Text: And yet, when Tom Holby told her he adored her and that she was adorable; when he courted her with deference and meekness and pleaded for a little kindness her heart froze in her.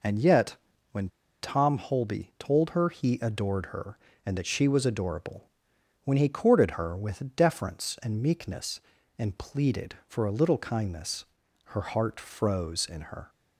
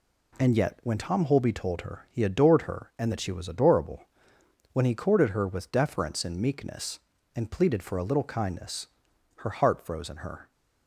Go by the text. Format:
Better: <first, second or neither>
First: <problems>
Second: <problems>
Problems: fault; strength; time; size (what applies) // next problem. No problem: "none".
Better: second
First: pauses between "when" and "Tom"; slight; at 1.0 s; 0.34 s long // pauses between "kindness" and "her"; at 11.2 s; 0.40 s long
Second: pauses between "kindness" and "her"; noticeable; at 8.8 s; 0.50 s long